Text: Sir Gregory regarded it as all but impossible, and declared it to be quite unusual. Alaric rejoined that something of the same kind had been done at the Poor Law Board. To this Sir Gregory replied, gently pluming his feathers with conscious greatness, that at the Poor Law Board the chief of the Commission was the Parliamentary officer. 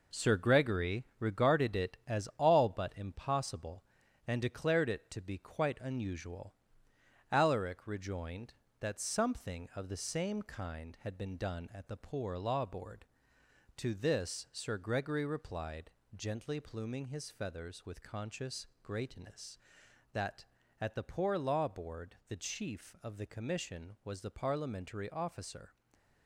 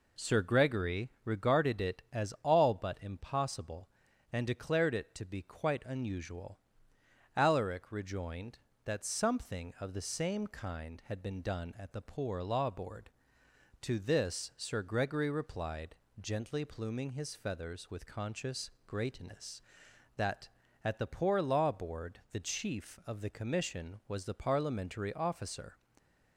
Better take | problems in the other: second | gets quieter; throughout; 7 dB // pauses between "conscious" and "greatness"; slight; at 18.6 s; 0.16 s long; slight in the second // stays silent after the last word; slight; from 25.6 s on; 0.6 s long

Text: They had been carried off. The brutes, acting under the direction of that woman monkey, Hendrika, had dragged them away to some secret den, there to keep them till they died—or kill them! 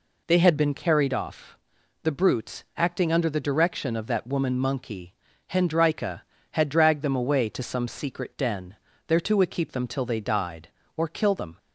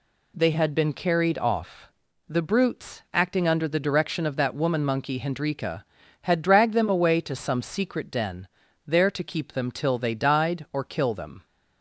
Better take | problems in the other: neither | none

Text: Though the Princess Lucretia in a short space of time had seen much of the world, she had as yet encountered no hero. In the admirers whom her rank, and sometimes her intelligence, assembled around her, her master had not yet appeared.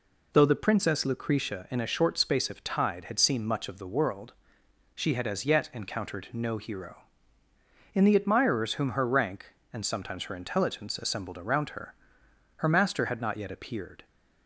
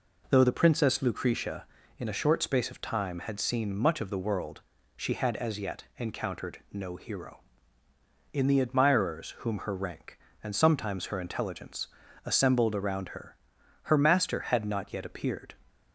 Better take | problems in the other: second | says "tide" for "time"; at 2.6 s

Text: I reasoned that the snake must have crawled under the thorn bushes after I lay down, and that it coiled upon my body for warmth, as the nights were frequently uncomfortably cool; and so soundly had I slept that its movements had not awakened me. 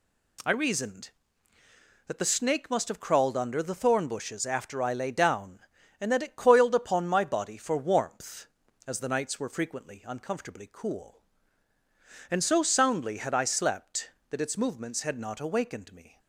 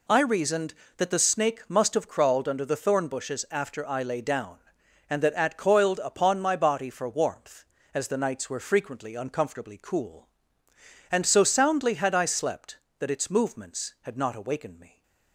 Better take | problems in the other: first | says "at" for "it"; at 5.3 s

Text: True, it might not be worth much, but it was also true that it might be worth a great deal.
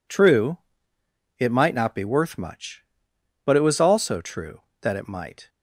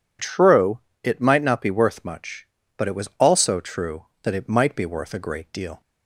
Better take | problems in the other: second | stops before "be worth a great deal"; at 5.4 s

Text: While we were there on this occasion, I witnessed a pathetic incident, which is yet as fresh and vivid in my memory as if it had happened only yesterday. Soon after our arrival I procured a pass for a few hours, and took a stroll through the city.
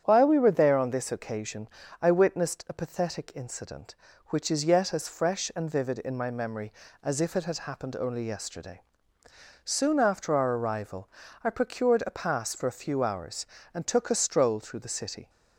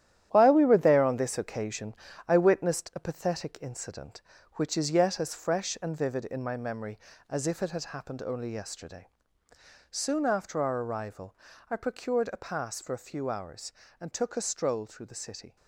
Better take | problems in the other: first | gets quieter; strong; throughout; 8.5 dB // starts louder than the rest; strong; until 1.3 s; 11.5 dB; strong in the first // pauses between "arrival" and "I"; slight; at 11.3 s; 0.34 s long; slight in the first

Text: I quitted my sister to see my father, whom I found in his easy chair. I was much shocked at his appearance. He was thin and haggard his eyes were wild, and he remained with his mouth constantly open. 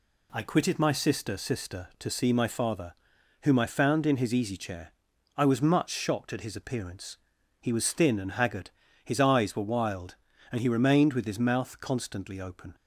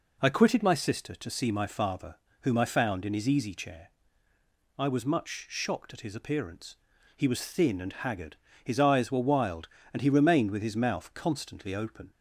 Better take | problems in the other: second | says "sister" twice; at 1.3 s // pauses between "haggard" and "his"; slight; at 8.7 s; 0.32 s long; slight in the second

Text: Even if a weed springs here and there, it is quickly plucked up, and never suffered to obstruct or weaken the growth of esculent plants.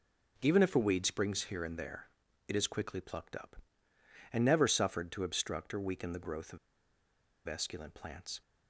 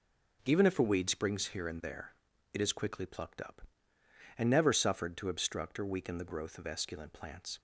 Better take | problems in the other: second | pauses between "of" and "esculent"; noticeable; at 6.5 s; 0.89 s long

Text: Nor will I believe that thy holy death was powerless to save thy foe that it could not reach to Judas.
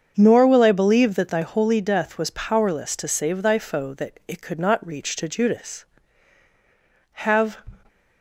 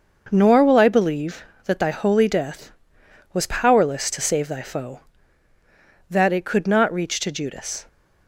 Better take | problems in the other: second | starts louder than the rest; until 1.1 s; 7 dB; noticeable in the second // goes on to say "Have"; slight; from 7.1 s on; 0.46 s long

